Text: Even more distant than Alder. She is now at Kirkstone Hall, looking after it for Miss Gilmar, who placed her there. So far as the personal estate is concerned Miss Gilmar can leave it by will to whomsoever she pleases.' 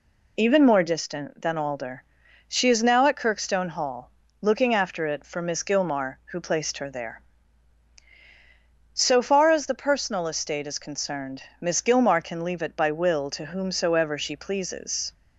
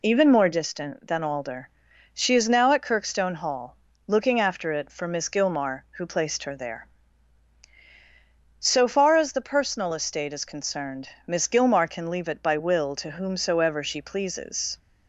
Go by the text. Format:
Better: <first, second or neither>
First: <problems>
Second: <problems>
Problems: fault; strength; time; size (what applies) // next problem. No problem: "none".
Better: neither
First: pauses between "concerned" and "Miss"; slight; at 11.4 s; 0.20 s long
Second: pauses between "concerned" and "Miss"; slight; at 11.0 s; 0.20 s long